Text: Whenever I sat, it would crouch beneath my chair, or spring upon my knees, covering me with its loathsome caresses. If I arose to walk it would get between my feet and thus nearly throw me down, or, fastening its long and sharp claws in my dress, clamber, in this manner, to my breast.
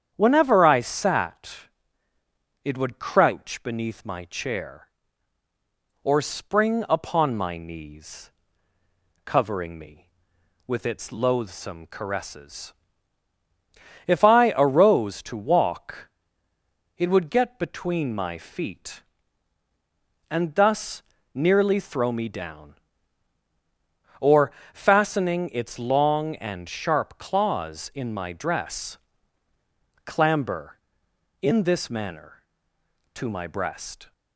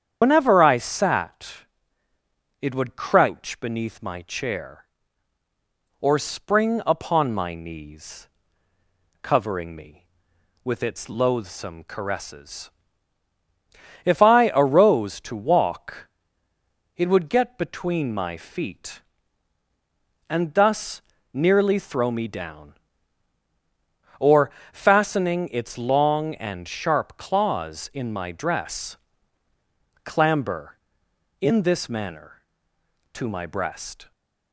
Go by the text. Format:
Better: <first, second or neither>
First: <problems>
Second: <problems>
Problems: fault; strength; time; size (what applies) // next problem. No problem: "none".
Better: first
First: starts louder than the rest; strong; until 1.1 s; 8.5 dB // pauses between "walk" and "it"; noticeable; at 16.1 s; 0.88 s long // pauses between "thus" and "nearly"; slight; at 21.0 s; 0.32 s long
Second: loses the start of "Whenever"; at 0.2 s; 95 ms // starts louder than the rest; strong; until 1.2 s; 8.5 dB // pauses between "walk" and "it"; noticeable; at 16.0 s; 0.88 s long // pauses between "thus" and "nearly"; slight; at 21.0 s; 0.32 s long